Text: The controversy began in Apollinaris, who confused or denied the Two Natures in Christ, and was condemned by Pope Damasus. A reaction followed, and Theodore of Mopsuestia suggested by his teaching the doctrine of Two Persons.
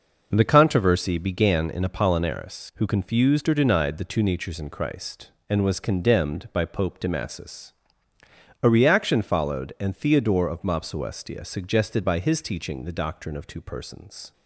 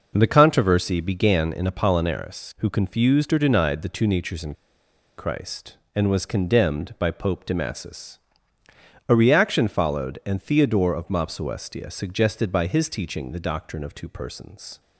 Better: first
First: none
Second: pauses between "in" and "Christ"; noticeable; at 4.5 s; 0.63 s long

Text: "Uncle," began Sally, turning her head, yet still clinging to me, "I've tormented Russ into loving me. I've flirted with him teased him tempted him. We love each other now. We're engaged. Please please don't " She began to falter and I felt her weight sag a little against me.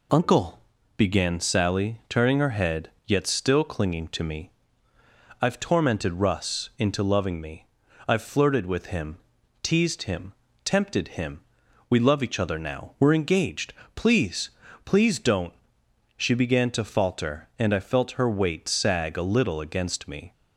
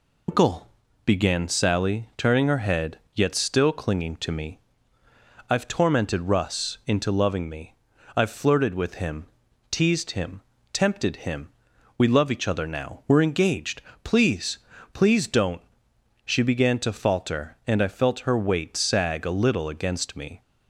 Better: first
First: pauses between "him" and "teased"; at 9.1 s; 0.44 s long // pauses between "him" and "tempted"; slight; at 10.3 s; 0.32 s long // pauses between "Please" and "please"; slight; at 14.4 s; 0.36 s long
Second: loses the start of "Uncle"; at 0.2 s; 105 ms // pauses between "him" and "teased"; at 9.2 s; 0.44 s long // pauses between "him" and "tempted"; slight; at 10.4 s; 0.32 s long // pauses between "Please" and "please"; slight; at 14.5 s; 0.36 s long

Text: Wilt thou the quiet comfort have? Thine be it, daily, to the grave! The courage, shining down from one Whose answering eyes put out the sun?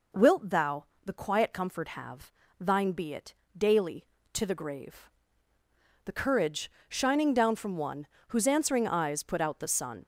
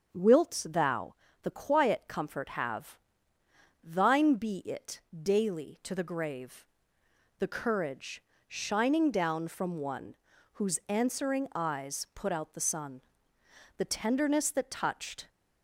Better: first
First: pauses between "thou" and "the"; slight; at 0.8 s; 0.20 s long // pauses between "one" and "Whose"; slight; at 8.0 s; 0.22 s long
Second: starts louder than the rest; until 1.1 s; 6.5 dB // pauses between "thou" and "the"; slight; at 1.1 s; 0.28 s long // pauses between "one" and "Whose"; at 10.1 s; 0.40 s long // goes on to say "The tenderness that touched"; from 13.7 s on; 1.5 s long

